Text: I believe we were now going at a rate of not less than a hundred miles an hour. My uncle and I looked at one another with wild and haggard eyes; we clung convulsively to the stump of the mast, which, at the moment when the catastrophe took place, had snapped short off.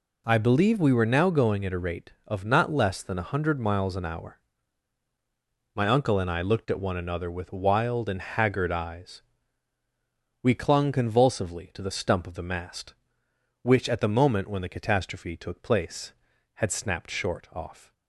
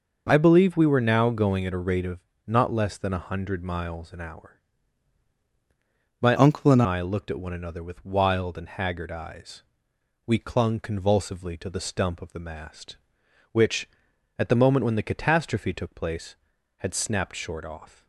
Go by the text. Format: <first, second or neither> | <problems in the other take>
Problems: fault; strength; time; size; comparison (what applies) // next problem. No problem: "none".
first | pauses between "of" and "not"; slight; at 2.2 s; 0.24 s long // changes voice from "uncle" to "and"; from 6.3 to 6.8 s; 0.5 s long